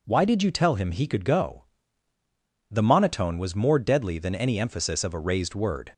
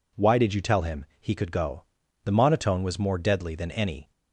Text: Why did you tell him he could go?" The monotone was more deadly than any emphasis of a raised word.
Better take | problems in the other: first | stops before "emphasis of a raised word"; at 4.1 s

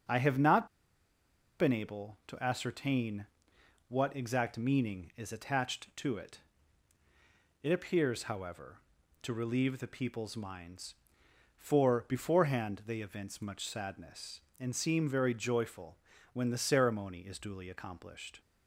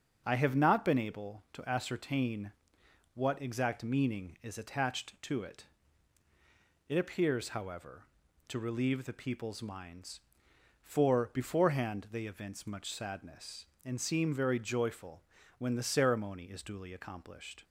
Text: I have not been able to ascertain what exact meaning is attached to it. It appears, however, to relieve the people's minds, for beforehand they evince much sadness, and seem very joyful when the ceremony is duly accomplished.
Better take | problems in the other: second | starts louder than the rest; until 2.0 s; 7 dB; also in the second // pauses between "not" and "been"; noticeable; at 0.6 s; 0.92 s long // pauses between "ascertain" and "what"; noticeable; at 3.2 s; 0.62 s long; noticeable in the second // pauses between "joyful" and "when"; slight; at 15.9 s; 0.34 s long; slight in the second

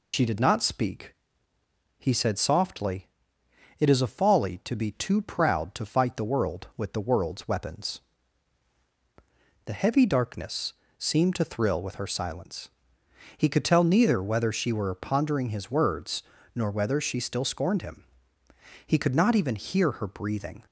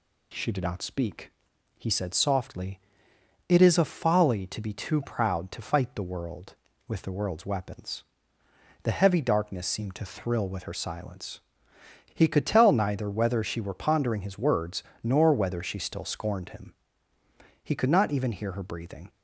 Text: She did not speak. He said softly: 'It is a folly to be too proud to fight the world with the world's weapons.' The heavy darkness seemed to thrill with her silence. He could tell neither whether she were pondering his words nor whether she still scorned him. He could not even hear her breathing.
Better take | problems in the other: second | loses the start of "She"; at 0.1 s; 100 ms // pauses between "darkness" and "seemed"; slight; at 10.7 s; 0.24 s long // pauses between "words" and "nor"; slight; at 16.2 s; 0.32 s long; slight in the second

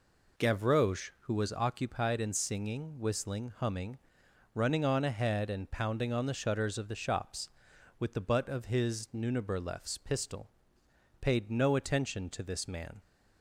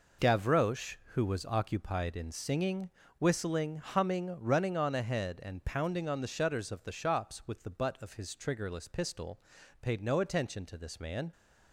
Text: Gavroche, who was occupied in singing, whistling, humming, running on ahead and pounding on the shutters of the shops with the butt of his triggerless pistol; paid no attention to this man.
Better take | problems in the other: second | says "nuniberlefs" for "triggerless"; at 9.1 s

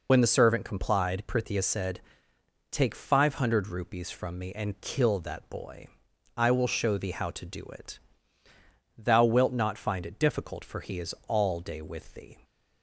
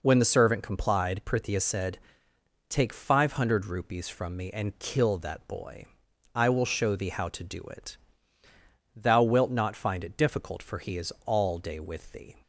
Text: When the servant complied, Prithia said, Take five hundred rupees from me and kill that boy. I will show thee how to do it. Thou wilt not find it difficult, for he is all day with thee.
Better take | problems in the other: second | loses the start of "When"; at 0.0 s; 65 ms

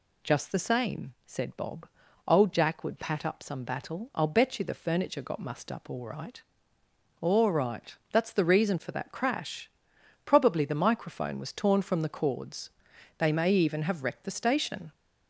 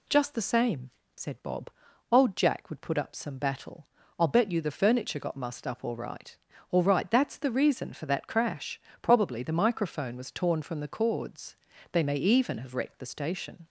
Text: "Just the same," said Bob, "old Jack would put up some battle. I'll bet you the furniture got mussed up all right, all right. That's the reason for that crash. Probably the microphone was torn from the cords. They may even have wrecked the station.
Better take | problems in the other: second | says "pat" for "put"; at 2.9 s

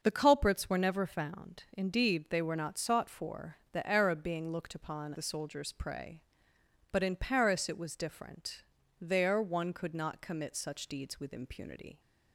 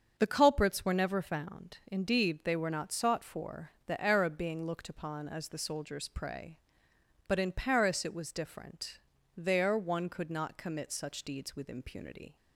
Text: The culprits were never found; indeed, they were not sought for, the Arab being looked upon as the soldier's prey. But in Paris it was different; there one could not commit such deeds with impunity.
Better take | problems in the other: second | starts louder than the rest; until 1.0 s; 6.5 dB; strong in the second // skips "as"; at 5.1 s

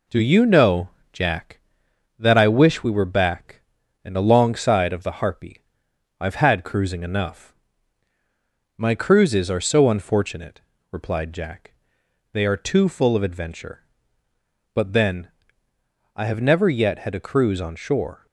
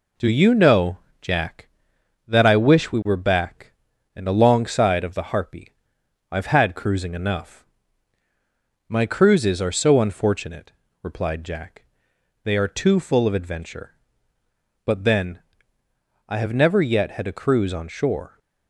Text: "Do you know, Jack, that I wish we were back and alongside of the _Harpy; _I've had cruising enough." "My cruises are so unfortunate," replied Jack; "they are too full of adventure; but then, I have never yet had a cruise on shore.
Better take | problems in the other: neither | none

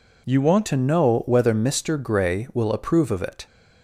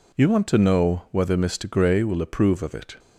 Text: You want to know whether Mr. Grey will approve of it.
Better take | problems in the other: second | changes voice at "to"; from 0.6 s on; 2.8 s long

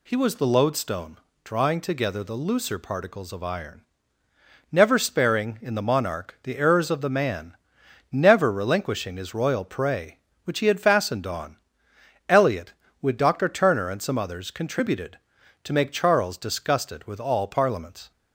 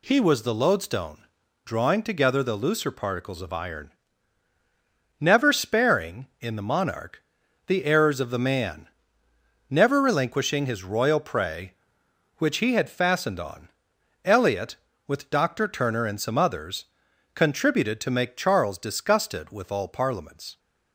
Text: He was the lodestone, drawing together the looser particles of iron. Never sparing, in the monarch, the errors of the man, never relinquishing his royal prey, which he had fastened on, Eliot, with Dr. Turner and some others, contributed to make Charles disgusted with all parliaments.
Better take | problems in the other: neither | none

